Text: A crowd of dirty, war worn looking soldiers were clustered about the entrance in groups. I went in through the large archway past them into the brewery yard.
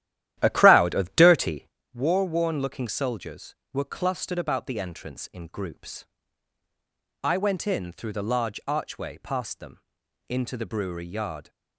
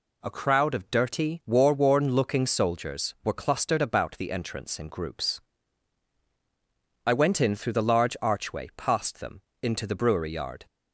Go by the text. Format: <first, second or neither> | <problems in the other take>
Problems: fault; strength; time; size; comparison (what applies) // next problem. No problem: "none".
second | starts louder than the rest; strong; until 1.8 s; 12.5 dB // pauses between "them" and "into"; noticeable; at 9.7 s; 0.48 s long; slight in the second